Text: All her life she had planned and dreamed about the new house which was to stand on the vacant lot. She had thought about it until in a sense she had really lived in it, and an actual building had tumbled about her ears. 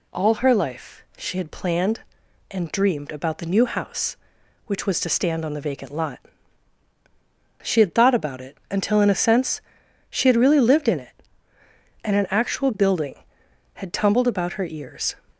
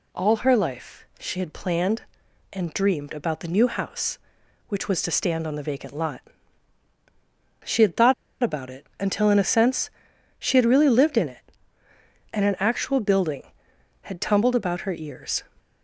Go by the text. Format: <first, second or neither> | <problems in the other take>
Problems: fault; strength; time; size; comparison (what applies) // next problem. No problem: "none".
first | pauses between "life" and "she"; slight; at 1.0 s; 0.16 s long; slight in the first // pauses between "thought" and "about"; slight; at 8.1 s; 0.29 s long // pauses between "sense" and "she"; noticeable; at 9.8 s; 0.48 s long; noticeable in the first